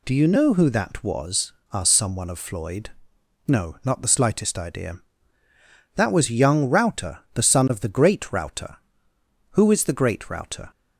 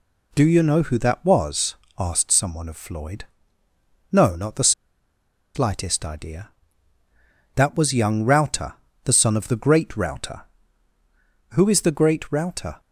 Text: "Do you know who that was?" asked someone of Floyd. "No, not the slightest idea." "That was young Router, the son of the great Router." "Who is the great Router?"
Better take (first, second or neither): first